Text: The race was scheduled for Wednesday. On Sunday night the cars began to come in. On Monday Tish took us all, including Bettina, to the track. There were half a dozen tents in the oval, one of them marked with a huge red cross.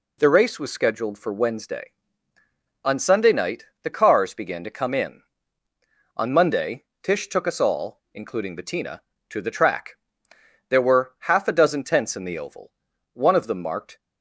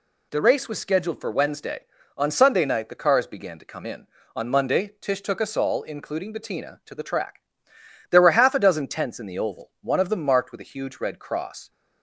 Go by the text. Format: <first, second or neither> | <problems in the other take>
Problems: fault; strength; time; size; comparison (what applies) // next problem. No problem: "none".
second | pauses between "night" and "the"; slight; at 3.6 s; 0.16 s long // pauses between "Monday" and "Tish"; slight; at 6.8 s; 0.18 s long // stops before "with a huge red cross"; at 13.9 s